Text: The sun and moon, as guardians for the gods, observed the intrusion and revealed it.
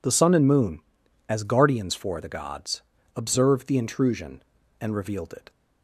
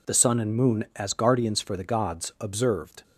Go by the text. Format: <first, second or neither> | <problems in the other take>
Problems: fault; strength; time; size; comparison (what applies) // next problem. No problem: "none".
first | stops before "the intrusion and revealed it"; at 3.0 s